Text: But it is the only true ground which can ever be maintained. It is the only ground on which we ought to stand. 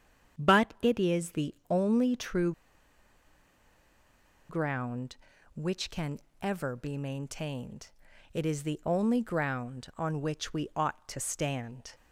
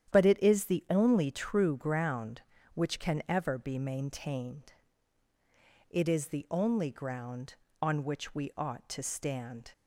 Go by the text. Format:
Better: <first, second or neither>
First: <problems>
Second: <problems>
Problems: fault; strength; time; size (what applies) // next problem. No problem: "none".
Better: second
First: starts louder than the rest; strong; until 1.4 s; 8.5 dB // pauses between "the" and "only"; slight; at 1.5 s; 0.16 s long // pauses between "true" and "ground"; strong; at 2.5 s; 1.9 s long // pauses between "can" and "ever"; slight; at 6.1 s; 0.24 s long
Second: starts louder than the rest; strong; until 1.1 s; 10 dB